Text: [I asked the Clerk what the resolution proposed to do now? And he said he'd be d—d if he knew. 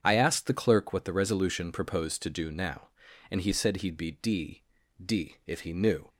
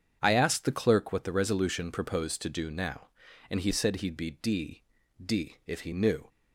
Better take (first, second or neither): neither